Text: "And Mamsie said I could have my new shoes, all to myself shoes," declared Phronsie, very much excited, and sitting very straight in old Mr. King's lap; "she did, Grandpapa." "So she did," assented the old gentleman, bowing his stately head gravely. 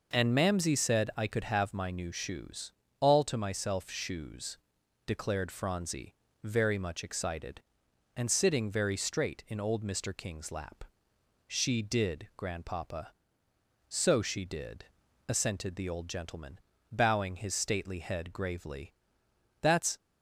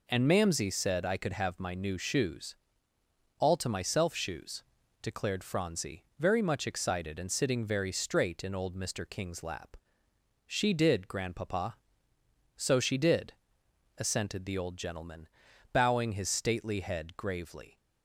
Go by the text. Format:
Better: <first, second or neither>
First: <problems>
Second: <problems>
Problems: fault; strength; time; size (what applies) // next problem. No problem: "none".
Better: second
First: goes on to say "That's"; slight; from 19.6 s on; 0.36 s long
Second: none